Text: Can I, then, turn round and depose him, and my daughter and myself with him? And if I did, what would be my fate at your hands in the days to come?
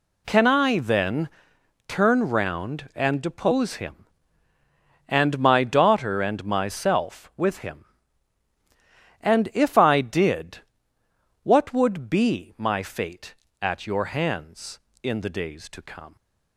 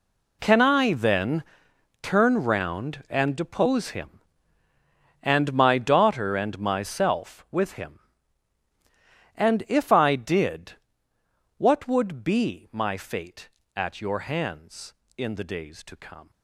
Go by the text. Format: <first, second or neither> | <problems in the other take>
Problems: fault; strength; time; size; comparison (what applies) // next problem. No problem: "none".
first | gets quieter; strong; throughout; 15 dB